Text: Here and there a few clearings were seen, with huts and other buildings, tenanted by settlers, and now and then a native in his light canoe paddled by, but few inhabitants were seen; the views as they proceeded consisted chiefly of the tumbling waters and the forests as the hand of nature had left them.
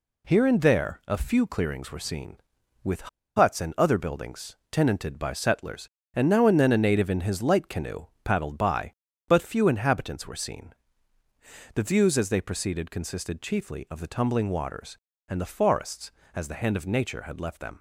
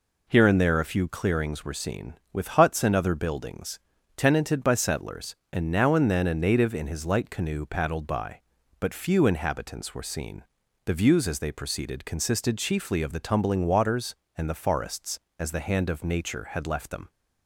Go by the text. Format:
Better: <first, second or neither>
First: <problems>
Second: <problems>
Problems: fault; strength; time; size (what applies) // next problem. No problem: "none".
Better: second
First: pauses between "with" and "huts"; slight; at 3.0 s; 0.29 s long // pauses between "canoe" and "paddled"; slight; at 8.0 s; 0.18 s long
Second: none